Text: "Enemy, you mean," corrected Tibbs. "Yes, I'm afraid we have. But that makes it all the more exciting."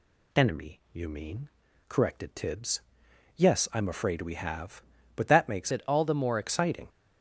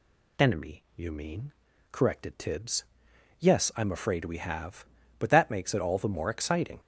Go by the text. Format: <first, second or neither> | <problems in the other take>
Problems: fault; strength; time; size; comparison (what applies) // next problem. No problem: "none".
second | changes voice from "it" to "more"; from 5.7 to 6.3 s; 0.6 s long